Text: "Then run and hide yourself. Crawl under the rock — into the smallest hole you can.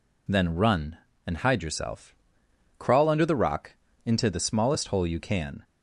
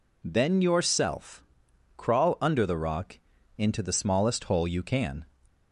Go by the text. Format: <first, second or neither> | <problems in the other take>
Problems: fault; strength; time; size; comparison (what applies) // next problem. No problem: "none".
first | skips "run and hide"; at 0.6 s